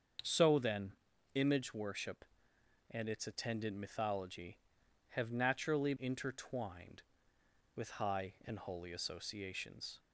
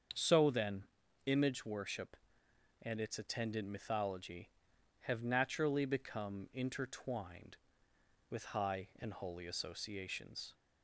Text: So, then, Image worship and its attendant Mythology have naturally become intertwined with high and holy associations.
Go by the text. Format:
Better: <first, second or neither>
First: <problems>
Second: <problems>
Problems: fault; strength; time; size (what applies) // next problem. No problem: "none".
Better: second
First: starts louder than the rest; until 1.6 s; 7 dB // skips "become"; at 5.9 s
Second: starts louder than the rest; until 1.5 s; 7 dB